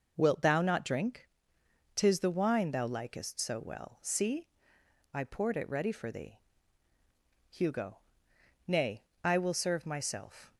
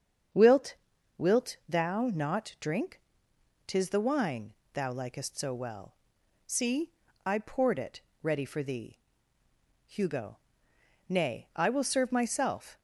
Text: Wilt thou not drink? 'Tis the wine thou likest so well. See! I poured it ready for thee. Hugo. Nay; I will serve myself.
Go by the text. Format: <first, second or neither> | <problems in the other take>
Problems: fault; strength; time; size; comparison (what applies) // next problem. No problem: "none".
first | starts louder than the rest; strong; until 1.8 s; 7.5 dB // says "Wilt" twice; at 1.1 s // pauses between "wine" and "thou"; slight; at 4.5 s; 0.22 s long // pauses between "it" and "ready"; slight; at 7.9 s; 0.24 s long